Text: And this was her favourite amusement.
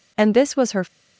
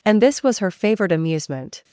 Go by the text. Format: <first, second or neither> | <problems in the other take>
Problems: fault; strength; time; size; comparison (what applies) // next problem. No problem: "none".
second | stops before "favourite amusement"; at 0.8 s